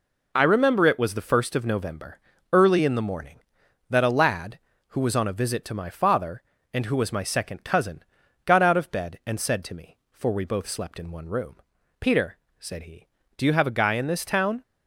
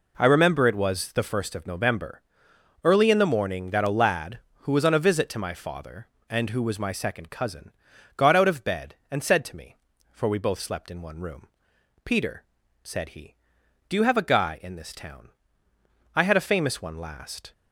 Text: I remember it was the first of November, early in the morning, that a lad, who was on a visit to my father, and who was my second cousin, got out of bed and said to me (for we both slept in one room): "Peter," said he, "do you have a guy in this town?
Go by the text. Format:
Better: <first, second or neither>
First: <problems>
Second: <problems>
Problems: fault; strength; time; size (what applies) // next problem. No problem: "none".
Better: first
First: none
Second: goes on to say "I had a famous one last"; from 16.1 s on; 1.3 s long